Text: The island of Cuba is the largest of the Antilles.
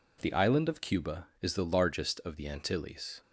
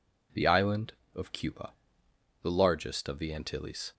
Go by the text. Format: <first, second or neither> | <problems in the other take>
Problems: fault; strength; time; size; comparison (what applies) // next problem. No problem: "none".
first | skips "is"; at 2.0 s